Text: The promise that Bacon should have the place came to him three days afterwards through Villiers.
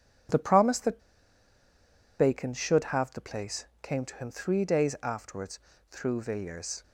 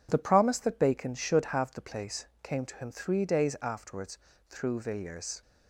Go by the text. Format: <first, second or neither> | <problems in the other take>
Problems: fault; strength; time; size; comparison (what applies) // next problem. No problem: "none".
second | pauses between "that" and "Bacon"; at 1.0 s; 1.1 s long // pauses between "place" and "came"; slight; at 3.6 s; 0.16 s long; slight in the second // pauses between "afterwards" and "through"; slight; at 5.5 s; 0.32 s long; slight in the second